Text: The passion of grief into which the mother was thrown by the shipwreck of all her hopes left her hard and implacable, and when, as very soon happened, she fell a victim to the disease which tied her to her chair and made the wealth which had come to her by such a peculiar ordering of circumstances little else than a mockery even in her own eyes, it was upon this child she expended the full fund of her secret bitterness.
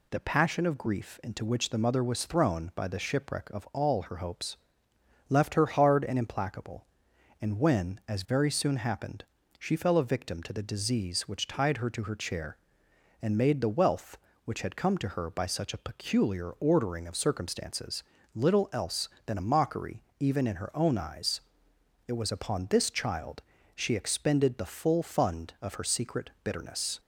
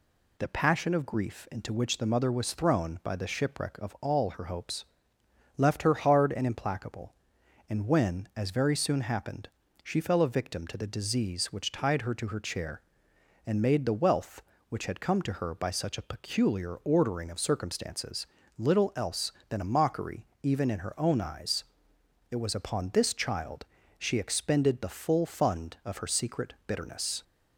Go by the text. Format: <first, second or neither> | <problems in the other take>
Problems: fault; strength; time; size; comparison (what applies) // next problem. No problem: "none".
neither | pauses between "hopes" and "left"; noticeable; the same in both // pauses between "circumstances" and "little"; slight; the same in both // pauses between "mockery" and "even"; slight; the same in both // pauses between "child" and "she"; slight; the same in both